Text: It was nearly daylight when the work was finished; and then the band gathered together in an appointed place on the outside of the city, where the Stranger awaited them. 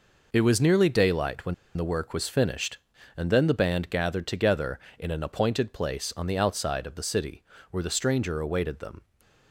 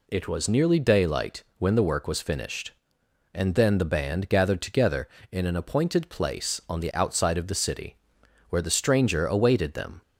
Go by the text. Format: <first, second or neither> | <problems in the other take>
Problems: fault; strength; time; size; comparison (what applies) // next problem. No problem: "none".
second | pauses between "when" and "the"; slight; at 1.5 s; 0.22 s long // stays silent after the last word; slight; from 8.9 s on; 0.6 s long